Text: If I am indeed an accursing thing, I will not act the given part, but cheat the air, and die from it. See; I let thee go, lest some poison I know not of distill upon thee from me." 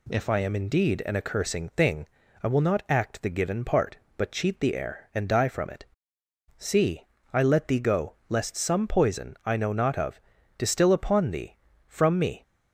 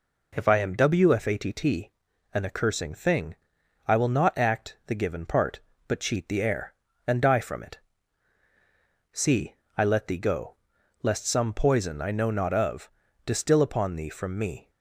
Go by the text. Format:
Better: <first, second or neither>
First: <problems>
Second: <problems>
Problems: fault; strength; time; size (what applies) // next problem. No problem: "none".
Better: first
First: pauses between "of" and "distill"; at 10.2 s; 0.38 s long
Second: says "wfatt" for "indeed"; at 0.7 s // pauses between "of" and "distill"; at 12.8 s; 0.38 s long